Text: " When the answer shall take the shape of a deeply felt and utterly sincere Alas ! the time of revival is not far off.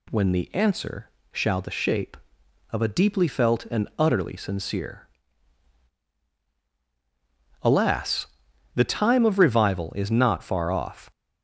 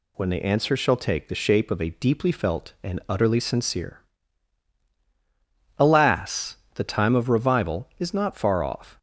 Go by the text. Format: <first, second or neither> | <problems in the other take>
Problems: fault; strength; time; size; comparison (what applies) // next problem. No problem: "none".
second | pauses between "answer" and "shall"; slight; at 1.1 s; 0.22 s long // skips "take"; at 1.6 s // pauses between "sincere" and "Alas"; strong; at 5.0 s; 2.5 s long; strong in the second